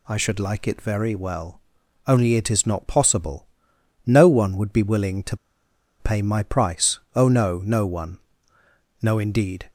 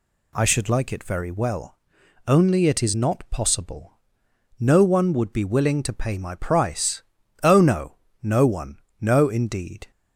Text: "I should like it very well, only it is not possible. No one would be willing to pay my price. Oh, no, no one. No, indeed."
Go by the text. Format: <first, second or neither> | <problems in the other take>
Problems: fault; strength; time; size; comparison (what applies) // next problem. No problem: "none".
second | pauses between "to" and "pay"; noticeable; at 5.3 s; 0.62 s long